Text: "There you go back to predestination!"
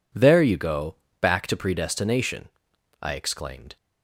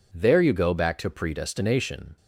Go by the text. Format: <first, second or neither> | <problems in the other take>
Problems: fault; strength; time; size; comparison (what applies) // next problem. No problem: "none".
second | pauses between "go" and "back"; slight; at 0.9 s; 0.26 s long // goes on to say "I exclaimed"; noticeable; from 3.0 s on; 0.76 s long